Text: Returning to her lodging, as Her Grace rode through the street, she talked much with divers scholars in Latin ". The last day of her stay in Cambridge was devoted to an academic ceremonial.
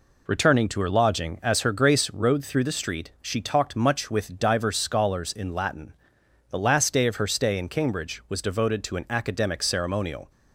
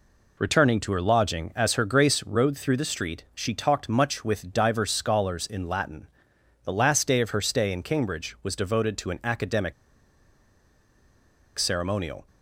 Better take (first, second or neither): first